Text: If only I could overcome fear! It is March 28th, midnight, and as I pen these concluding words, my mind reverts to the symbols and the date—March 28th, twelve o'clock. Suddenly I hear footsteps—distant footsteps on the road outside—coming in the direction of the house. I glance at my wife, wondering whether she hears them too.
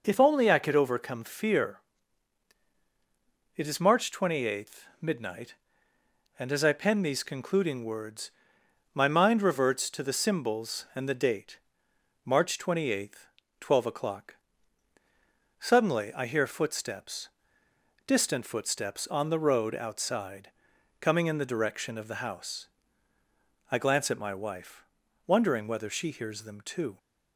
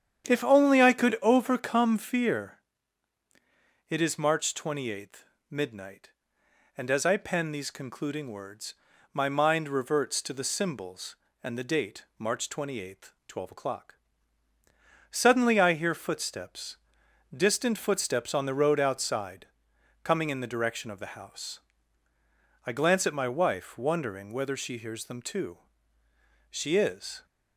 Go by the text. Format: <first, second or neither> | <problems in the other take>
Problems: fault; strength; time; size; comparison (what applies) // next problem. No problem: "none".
first | starts louder than the rest; strong; until 1.3 s; 9 dB // goes on to say "She is"; noticeable; from 26.4 s on; 0.76 s long